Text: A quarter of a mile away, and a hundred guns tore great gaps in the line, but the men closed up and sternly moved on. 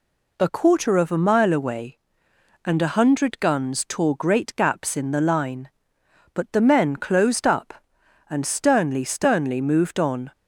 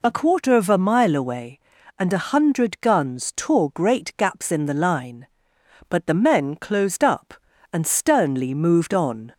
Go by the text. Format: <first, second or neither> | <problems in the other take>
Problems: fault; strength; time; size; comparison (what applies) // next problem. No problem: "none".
second | says "sternly" twice; at 9.0 s